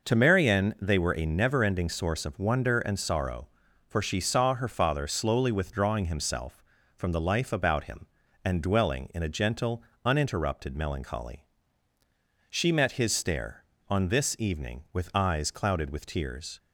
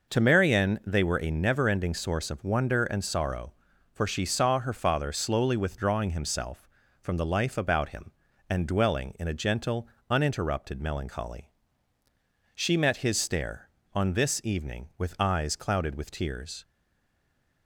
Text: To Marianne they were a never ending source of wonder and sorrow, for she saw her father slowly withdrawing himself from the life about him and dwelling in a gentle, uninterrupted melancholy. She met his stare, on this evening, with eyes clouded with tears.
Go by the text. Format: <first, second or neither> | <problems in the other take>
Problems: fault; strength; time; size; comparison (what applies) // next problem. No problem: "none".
first | stays silent after the last word; from 16.6 s on; 1.0 s long